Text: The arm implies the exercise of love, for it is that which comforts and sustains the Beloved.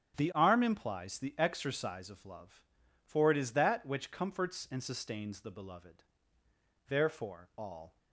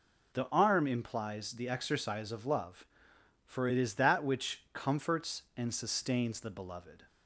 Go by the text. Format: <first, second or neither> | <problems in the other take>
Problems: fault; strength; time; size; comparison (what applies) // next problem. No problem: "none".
second | starts louder than the rest; strong; until 1.2 s; 8 dB // goes on to say "Therefore all"; noticeable; from 6.8 s on; 1.1 s long